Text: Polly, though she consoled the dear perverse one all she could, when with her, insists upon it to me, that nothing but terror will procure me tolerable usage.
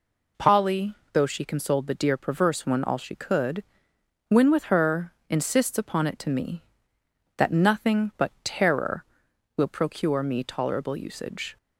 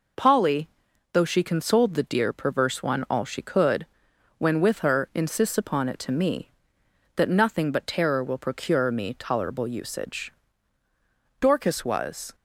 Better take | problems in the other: first | goes on to say "Dorcas was"; noticeable; from 11.4 s on; 0.94 s long

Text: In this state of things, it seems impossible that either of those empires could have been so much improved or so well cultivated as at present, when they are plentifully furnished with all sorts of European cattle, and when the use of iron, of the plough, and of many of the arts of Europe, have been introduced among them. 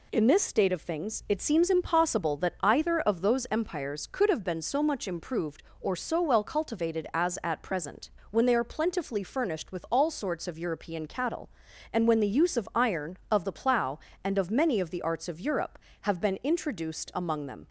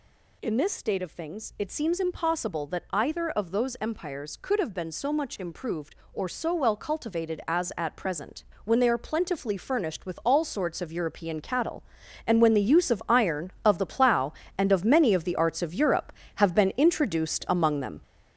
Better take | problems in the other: first | gets louder; throughout; 6.5 dB

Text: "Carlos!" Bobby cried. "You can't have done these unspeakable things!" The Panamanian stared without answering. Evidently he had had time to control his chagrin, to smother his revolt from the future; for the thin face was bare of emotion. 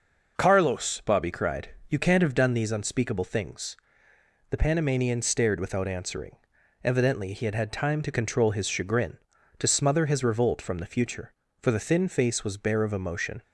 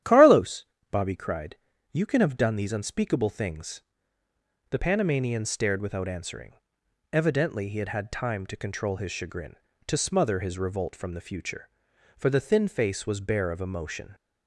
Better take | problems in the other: first | starts louder than the rest; strong; until 1.3 s; 11 dB // says "can" for "can't"; at 2.0 s

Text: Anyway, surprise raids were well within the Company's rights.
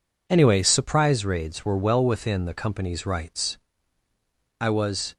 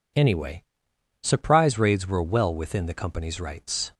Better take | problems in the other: second | goes on to say "I was"; from 4.5 s on; 0.56 s long

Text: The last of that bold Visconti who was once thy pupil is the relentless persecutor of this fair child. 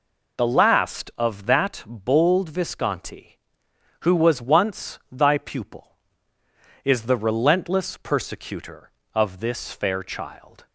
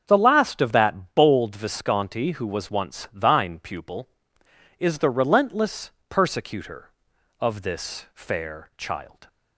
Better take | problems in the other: first | starts louder than the rest; until 1.0 s; 7 dB // says "thine" for "thy"; at 3.1 s // pauses between "relentless" and "persecutor"; slight; at 5.9 s; 0.18 s long

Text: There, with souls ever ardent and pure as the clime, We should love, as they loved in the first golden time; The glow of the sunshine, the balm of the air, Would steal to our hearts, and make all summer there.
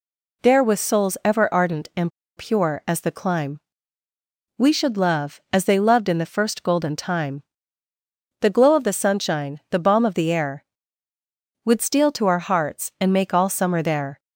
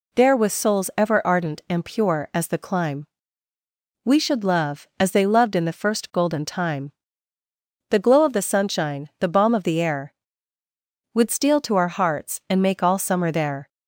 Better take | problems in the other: second | pauses between "and" and "pure"; slight; at 2.1 s; 0.28 s long

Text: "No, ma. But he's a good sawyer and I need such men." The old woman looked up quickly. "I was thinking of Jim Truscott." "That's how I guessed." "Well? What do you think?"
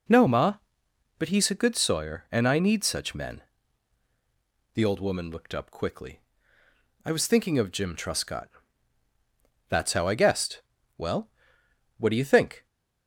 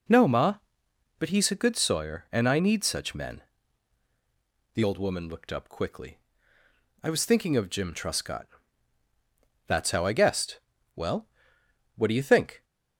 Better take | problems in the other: neither | none

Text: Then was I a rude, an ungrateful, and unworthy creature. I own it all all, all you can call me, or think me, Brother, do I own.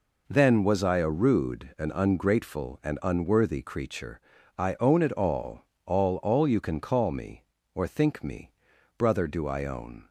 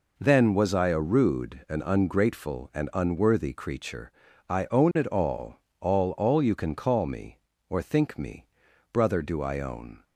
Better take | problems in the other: neither | pauses between "all" and "all"; slight; the same in both

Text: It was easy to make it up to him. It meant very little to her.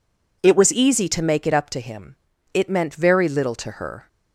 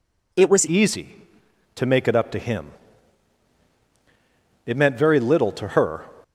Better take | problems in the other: first | changes voice at "easy"; from 0.6 s on; 5.4 s long

